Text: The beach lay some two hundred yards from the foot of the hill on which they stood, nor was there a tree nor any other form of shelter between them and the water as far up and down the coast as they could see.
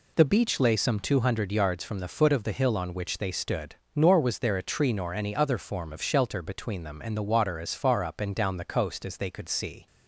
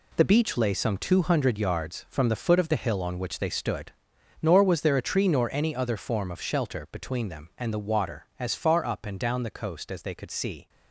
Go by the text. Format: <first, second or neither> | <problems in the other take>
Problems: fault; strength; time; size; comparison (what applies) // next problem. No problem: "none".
first | gets quieter; strong; throughout; 9 dB